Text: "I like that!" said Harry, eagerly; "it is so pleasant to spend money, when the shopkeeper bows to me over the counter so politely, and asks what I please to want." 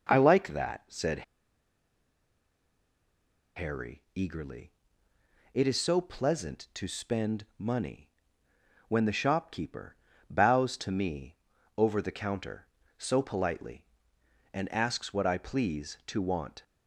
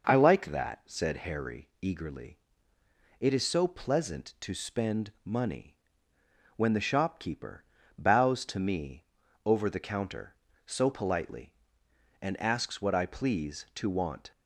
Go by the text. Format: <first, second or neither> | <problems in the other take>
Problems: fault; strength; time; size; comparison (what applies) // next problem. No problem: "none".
second | pauses between "said" and "Harry"; strong; at 1.2 s; 2.3 s long // pauses between "shopkeeper" and "bows"; slight; at 9.9 s; 0.32 s long; slight in the second // pauses between "me" and "over"; at 11.3 s; 0.42 s long; also in the second